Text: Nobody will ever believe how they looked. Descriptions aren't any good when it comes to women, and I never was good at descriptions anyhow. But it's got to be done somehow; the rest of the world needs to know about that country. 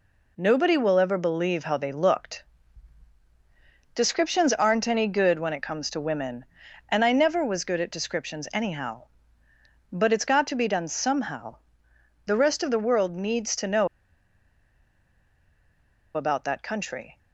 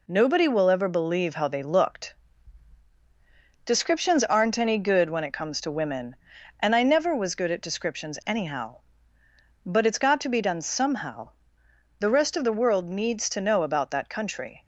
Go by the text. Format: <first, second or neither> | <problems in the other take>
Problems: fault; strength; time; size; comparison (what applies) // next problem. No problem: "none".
second | pauses between "know" and "about"; strong; at 13.8 s; 2.2 s long